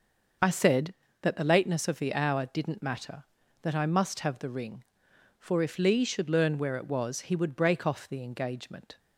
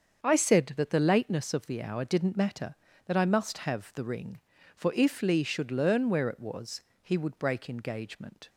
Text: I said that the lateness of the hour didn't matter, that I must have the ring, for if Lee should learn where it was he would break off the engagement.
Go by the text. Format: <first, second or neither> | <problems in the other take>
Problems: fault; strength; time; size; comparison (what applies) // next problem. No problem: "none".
first | starts louder than the rest; until 1.2 s; 7 dB; noticeable in the first // pauses between "was" and "he"; slight; at 6.8 s; 0.22 s long // skips "off the"; at 7.6 s